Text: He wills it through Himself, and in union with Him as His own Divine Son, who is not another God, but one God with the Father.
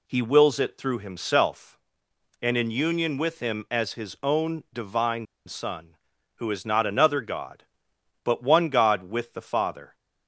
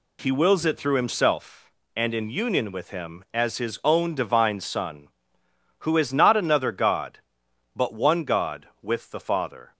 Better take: second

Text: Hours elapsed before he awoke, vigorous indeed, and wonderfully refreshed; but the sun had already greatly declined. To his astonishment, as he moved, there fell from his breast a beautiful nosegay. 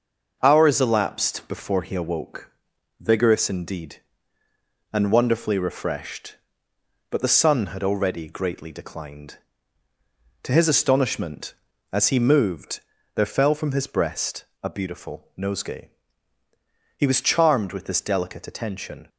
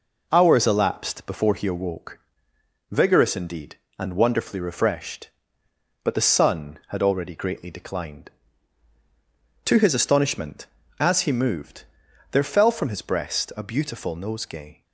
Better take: second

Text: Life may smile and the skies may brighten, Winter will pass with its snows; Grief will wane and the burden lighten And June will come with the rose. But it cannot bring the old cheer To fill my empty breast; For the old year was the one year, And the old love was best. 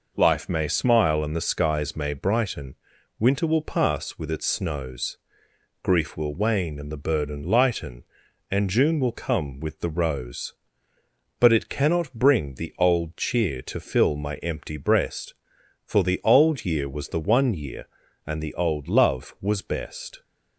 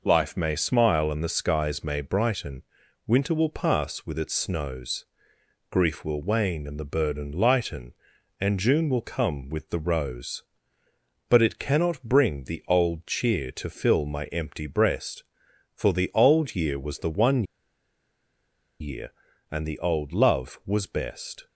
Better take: first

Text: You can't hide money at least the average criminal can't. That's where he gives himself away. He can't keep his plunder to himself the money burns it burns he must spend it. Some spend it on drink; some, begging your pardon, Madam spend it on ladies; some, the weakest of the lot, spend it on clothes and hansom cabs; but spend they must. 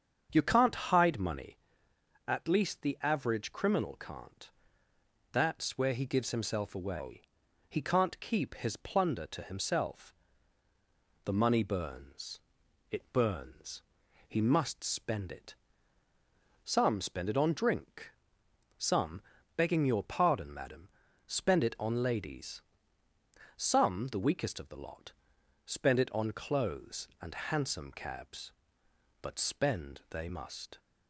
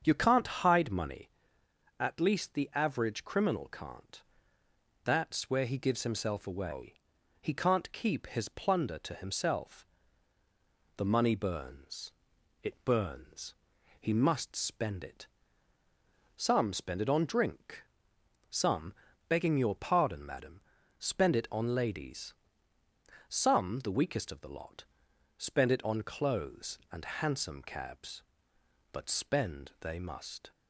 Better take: neither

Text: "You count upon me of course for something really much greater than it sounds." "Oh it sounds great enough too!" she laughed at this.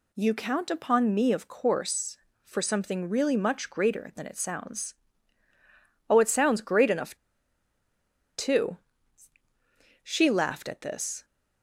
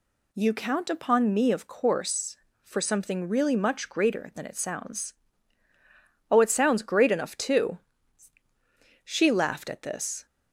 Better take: second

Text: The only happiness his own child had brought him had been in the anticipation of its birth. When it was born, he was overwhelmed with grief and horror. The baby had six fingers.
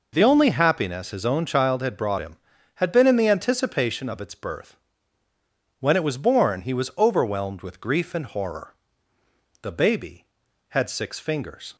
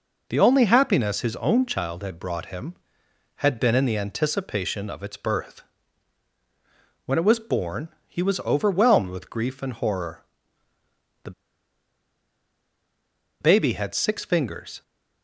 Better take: first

